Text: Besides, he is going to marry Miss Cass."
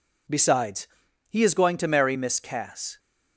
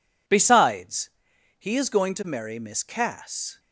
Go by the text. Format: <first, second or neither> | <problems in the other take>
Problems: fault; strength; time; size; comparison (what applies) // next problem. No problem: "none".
neither | none